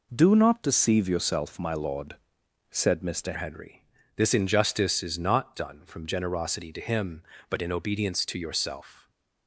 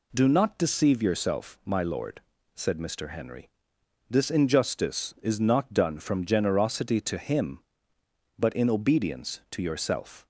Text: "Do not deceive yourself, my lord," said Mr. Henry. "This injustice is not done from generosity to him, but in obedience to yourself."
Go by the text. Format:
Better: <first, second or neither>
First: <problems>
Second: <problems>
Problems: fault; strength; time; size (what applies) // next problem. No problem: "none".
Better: second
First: changes voice at "Henry"; from 3.3 s on; 5.7 s long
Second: none